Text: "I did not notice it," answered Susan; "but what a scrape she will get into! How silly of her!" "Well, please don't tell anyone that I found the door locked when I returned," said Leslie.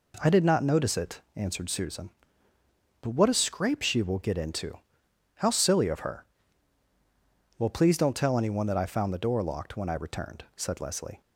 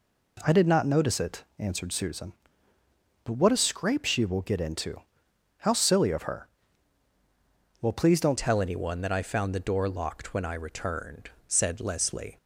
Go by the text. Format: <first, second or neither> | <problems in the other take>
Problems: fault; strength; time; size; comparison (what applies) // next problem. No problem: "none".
first | changes voice at "tell"; from 8.3 s on; 4.0 s long